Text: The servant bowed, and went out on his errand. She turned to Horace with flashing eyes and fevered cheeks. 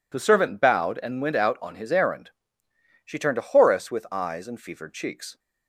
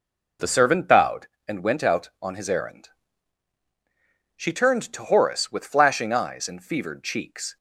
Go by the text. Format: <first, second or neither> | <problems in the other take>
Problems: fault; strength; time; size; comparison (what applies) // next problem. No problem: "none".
second | skips "flashing"; at 4.0 s